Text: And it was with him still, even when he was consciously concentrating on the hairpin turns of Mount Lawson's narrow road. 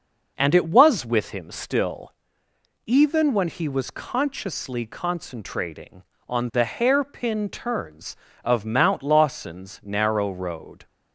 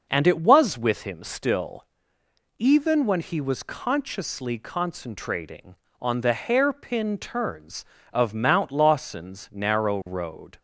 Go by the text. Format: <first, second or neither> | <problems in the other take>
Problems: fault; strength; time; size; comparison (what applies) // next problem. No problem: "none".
neither | none